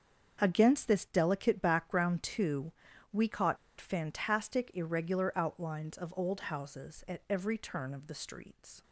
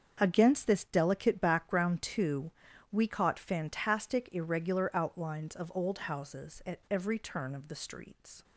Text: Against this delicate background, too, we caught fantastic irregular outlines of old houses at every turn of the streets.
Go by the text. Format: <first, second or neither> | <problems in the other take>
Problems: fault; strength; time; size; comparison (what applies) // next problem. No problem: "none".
second | starts louder than the rest; until 1.4 s; 7 dB; also in the second // pauses between "caught" and "fantastic"; slight; at 3.5 s; 0.23 s long